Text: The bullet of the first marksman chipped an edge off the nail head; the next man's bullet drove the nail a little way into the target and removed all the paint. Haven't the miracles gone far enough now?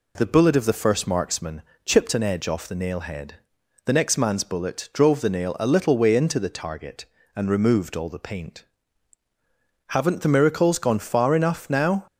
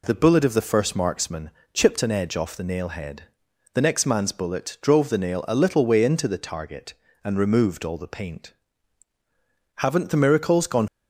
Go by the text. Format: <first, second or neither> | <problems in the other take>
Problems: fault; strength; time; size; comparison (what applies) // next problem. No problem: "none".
first | pauses between "marksman" and "chipped"; slight; at 1.4 s; 0.24 s long; slight in the first // stops before "far enough now"; at 10.8 s